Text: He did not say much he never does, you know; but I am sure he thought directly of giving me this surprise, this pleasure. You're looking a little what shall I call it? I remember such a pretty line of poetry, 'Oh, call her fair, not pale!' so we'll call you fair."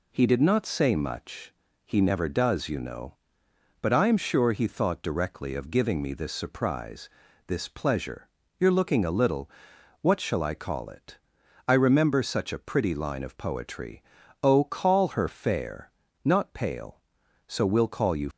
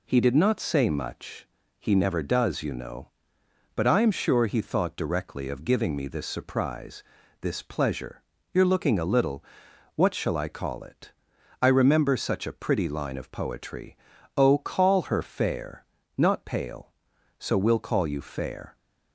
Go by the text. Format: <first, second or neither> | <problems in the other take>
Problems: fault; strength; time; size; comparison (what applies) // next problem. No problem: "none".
second | pauses between "much" and "he"; slight; at 1.5 s; 0.32 s long; slight in the second // pauses between "little" and "what"; noticeable; at 9.4 s; 0.52 s long; noticeable in the second // stops before "fair"; at 18.3 s